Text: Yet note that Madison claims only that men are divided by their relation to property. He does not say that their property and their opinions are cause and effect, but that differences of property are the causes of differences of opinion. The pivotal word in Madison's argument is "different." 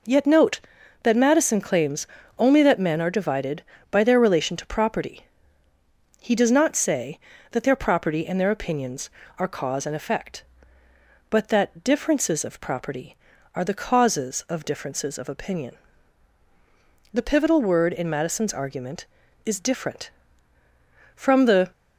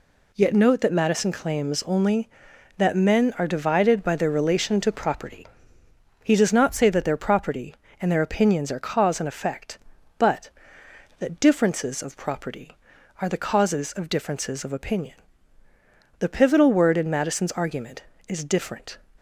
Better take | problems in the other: second | pauses between "claims" and "only"; slight; at 2.0 s; 0.32 s long // goes on to say "From the"; from 21.1 s on; 0.56 s long

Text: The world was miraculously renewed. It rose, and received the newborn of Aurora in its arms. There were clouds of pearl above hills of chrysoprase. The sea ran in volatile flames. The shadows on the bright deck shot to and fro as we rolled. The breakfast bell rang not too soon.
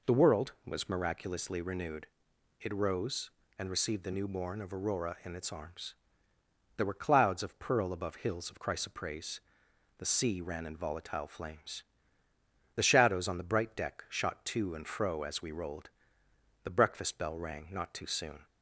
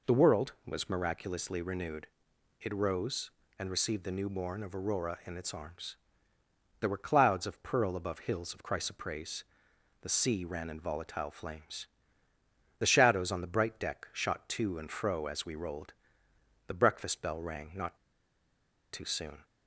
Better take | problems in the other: first | pauses between "not" and "too"; noticeable; at 17.9 s; 0.97 s long

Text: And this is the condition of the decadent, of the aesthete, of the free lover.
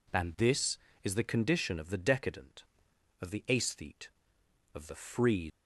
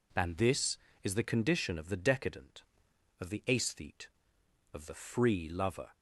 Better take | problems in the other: second | stops before "lover"; at 5.4 s

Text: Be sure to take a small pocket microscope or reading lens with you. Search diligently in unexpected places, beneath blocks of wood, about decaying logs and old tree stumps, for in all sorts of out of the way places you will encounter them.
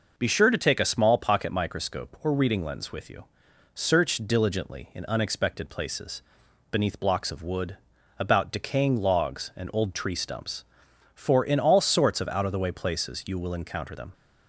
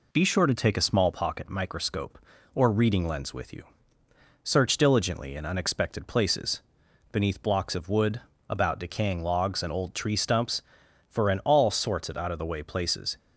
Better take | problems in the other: first | stops before "you will encounter them"; at 13.1 s

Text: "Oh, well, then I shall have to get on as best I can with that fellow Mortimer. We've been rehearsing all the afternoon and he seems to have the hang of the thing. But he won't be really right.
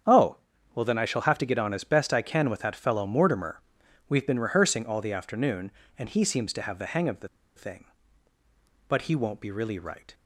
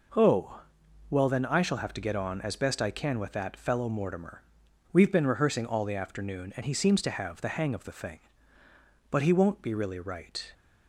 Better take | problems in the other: second | starts louder than the rest; strong; until 1.4 s; 8 dB // pauses between "the" and "thing"; slight; at 7.2 s; 0.27 s long

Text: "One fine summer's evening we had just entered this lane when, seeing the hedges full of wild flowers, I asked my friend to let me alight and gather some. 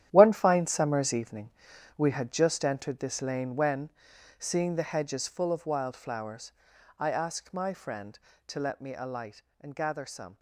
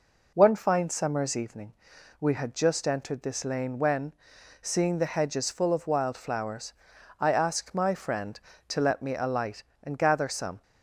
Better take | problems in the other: second | gets quieter; strong; throughout; 11 dB // pauses between "evening" and "we"; noticeable; at 1.5 s; 0.46 s long; noticeable in the second

